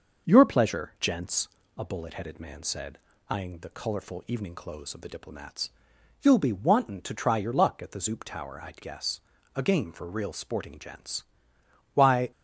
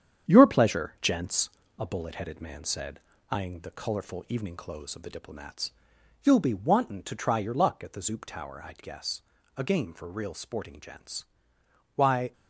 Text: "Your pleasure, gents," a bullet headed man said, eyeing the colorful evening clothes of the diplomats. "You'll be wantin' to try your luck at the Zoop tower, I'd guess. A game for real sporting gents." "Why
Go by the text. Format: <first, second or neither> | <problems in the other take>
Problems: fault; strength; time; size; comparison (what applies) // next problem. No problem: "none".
first | gets quieter; noticeable; throughout; 6 dB